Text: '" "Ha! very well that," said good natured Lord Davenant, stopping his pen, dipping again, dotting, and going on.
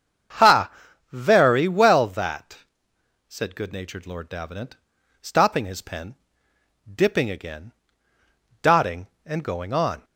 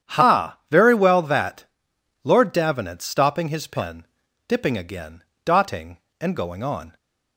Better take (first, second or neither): first